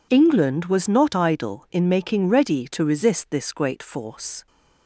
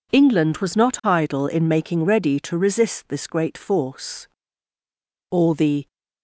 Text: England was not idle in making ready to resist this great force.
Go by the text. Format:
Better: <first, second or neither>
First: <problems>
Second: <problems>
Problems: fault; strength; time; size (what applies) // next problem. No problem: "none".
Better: first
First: none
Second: goes on to say "All the"; noticeable; from 5.3 s on; 0.62 s long